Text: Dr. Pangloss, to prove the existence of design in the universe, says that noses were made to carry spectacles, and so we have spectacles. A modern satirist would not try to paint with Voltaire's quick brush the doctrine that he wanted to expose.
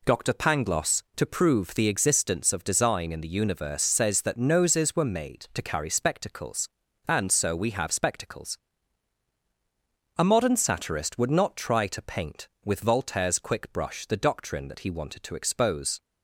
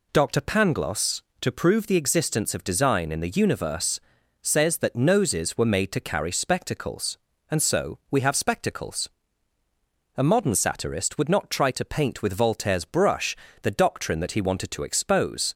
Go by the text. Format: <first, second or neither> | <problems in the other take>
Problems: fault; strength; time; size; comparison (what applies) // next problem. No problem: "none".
first | skips "quick"; at 12.8 s // pauses between "brush" and "the"; slight; at 13.3 s; 0.26 s long